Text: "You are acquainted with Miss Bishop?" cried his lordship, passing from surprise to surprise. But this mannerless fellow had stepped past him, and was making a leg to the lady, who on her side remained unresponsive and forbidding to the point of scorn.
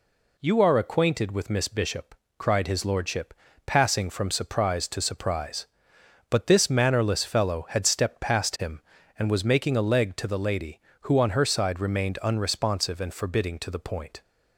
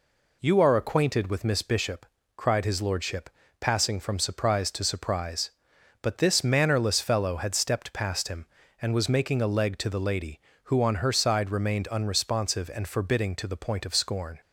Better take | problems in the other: second | stops before "of scorn"; at 14.2 s

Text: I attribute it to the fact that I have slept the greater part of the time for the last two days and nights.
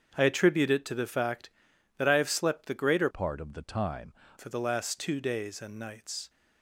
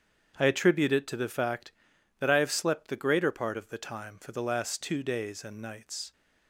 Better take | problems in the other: second | starts louder than the rest; strong; until 1.1 s; 7.5 dB; strong in the second // changes voice from "part" to "time"; from 3.1 to 4.1 s; 1.0 s long

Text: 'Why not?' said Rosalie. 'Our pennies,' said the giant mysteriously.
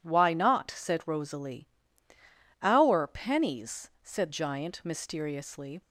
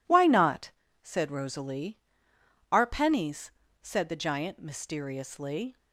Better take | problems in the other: second | skips "the"; at 4.2 s

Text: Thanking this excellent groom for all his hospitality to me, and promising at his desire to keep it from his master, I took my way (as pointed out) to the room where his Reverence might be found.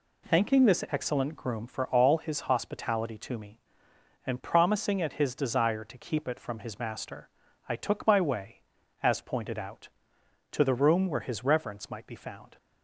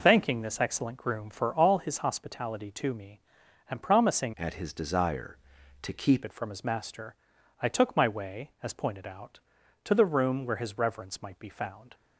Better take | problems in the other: first | changes voice from "at" to "keep"; from 4.3 to 6.2 s; 1.9 s long

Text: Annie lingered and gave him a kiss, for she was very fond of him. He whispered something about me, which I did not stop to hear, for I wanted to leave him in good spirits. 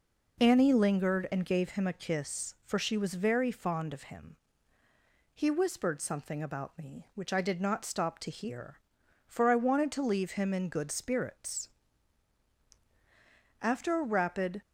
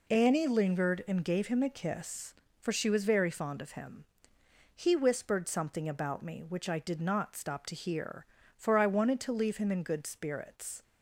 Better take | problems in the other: second | goes on to say "After a rapid"; noticeable; from 13.6 s on; 1.0 s long

